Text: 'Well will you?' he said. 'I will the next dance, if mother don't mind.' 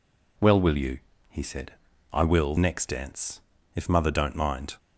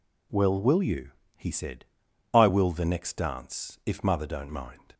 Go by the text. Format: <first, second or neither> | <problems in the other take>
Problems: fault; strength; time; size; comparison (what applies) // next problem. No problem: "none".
second | skips "the"; at 2.5 s